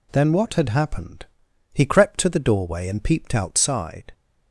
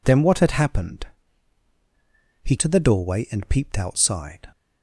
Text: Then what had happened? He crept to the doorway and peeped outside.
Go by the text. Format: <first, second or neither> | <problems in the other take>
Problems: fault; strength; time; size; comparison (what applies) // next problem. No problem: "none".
first | skips "crept"; at 2.5 s